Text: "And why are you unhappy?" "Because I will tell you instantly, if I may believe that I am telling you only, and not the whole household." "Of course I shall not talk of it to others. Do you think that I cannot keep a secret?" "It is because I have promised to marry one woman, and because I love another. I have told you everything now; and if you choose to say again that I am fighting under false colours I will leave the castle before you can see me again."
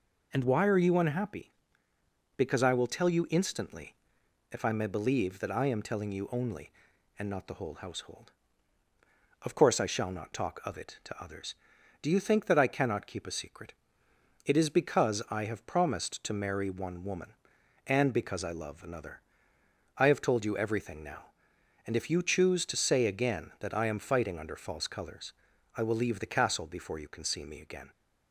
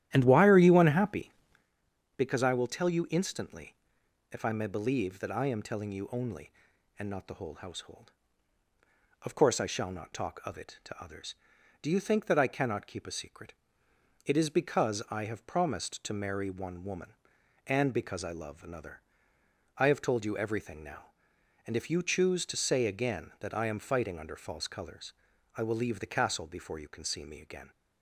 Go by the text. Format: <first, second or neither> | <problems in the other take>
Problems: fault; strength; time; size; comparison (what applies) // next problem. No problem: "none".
first | starts louder than the rest; strong; until 1.7 s; 12.5 dB // pauses between "colours" and "I"; at 25.1 s; 0.42 s long; also in the first